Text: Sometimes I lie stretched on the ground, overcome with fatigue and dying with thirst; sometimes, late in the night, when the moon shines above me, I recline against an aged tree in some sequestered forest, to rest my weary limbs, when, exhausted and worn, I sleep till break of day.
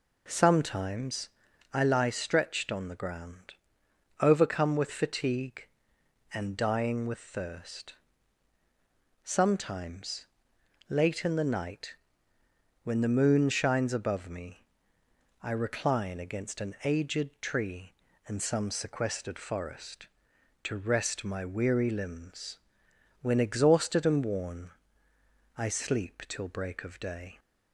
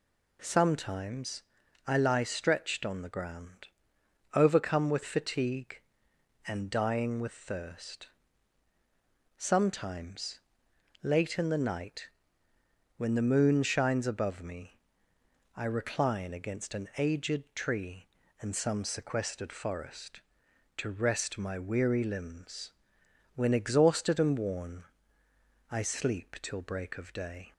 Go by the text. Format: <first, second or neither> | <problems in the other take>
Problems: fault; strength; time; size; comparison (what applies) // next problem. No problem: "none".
second | starts louder than the rest; until 1.8 s; 4 dB // pauses between "Sometimes" and "I"; at 1.2 s; 0.44 s long; also in the second